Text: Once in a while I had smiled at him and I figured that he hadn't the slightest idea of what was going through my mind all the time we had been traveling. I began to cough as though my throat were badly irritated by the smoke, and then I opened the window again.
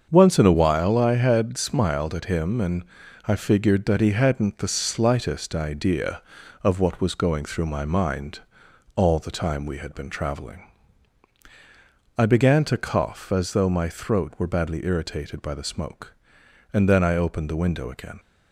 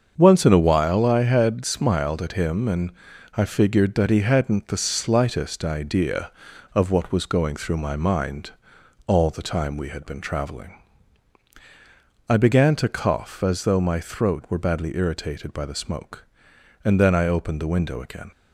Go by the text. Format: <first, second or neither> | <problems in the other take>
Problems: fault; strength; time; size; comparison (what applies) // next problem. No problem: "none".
neither | starts louder than the rest; the same in both // pauses between "and" and "I"; the same in both // pauses between "mind" and "all"; noticeable; the same in both